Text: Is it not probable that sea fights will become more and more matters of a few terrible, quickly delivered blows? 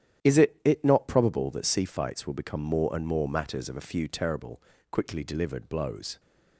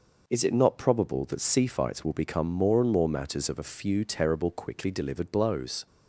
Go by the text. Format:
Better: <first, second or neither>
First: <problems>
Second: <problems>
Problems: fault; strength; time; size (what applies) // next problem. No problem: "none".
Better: second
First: starts louder than the rest; strong; until 1.3 s; 10 dB // says "it" twice; at 0.6 s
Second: none